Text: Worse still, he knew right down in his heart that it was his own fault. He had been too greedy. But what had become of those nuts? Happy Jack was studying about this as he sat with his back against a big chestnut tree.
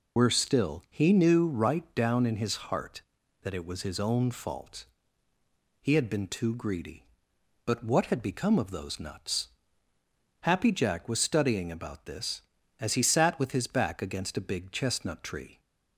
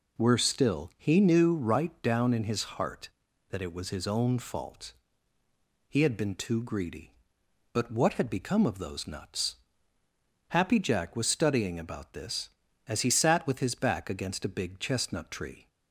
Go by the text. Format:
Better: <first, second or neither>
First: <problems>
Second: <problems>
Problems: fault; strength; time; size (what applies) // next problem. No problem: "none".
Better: second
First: loses the start of "Worse"; at 0.1 s; 65 ms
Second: none